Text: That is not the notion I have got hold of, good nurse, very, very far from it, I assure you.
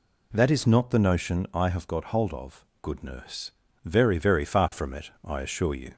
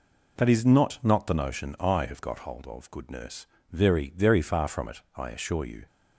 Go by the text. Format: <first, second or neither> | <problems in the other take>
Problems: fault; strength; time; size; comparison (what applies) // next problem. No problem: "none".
first | says "not" twice; at 1.0 s